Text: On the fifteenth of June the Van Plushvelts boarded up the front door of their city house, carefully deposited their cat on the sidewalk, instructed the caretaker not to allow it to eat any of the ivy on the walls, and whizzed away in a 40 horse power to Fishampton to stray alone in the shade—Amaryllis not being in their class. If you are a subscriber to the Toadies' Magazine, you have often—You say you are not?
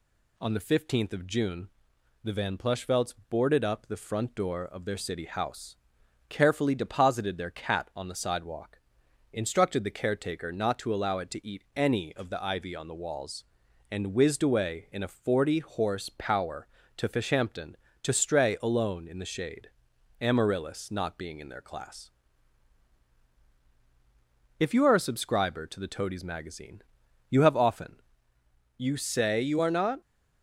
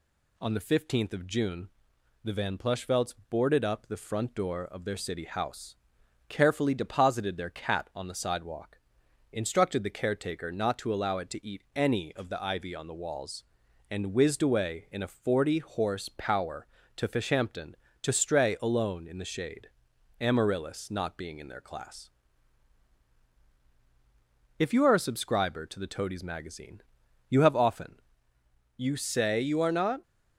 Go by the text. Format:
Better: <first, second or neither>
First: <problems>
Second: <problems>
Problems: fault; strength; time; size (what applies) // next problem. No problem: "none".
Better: neither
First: pauses between "June" and "the"; noticeable; at 1.6 s; 0.54 s long // pauses between "Plushvelts" and "boarded"; slight; at 3.1 s; 0.16 s long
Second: pauses between "June" and "the"; noticeable; at 1.6 s; 0.54 s long // pauses between "Plushvelts" and "boarded"; slight; at 3.1 s; 0.16 s long